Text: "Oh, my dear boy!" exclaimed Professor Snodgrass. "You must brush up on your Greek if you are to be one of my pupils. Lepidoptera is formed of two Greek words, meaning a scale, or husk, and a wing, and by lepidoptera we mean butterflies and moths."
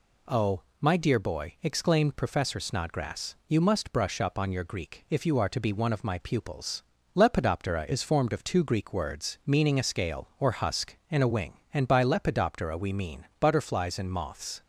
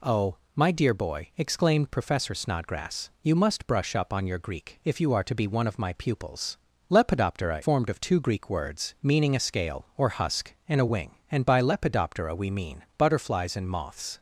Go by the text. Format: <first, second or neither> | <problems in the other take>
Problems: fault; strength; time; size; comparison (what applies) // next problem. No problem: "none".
first | skips "is"; at 7.6 s